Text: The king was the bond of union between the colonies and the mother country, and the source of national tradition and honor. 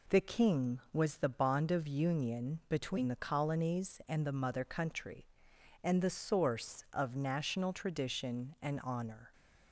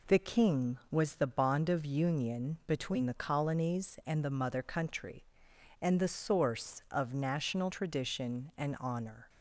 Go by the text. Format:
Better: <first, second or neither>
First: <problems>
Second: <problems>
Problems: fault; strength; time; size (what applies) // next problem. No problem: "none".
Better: neither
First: none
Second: none